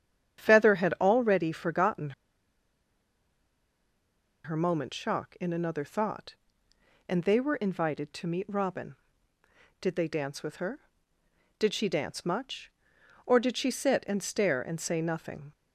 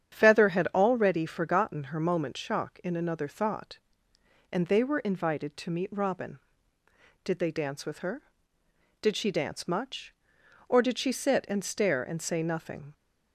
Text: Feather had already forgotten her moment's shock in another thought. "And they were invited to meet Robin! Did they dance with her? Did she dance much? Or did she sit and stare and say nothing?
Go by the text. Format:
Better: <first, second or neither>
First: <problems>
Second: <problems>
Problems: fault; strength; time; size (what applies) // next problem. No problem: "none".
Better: second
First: starts louder than the rest; strong; until 1.4 s; 9 dB // pauses between "forgotten" and "her"; strong; at 2.1 s; 2.3 s long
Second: starts louder than the rest; strong; until 1.2 s; 9 dB